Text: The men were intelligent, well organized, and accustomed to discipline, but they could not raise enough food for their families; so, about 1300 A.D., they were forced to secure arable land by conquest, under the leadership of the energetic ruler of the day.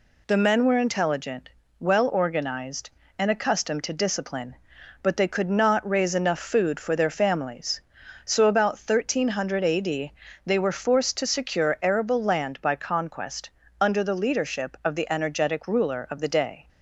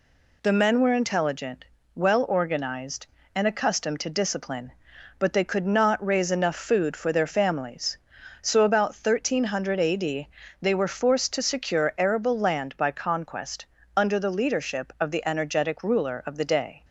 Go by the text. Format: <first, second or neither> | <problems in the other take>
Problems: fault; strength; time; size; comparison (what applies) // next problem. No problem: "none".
neither | none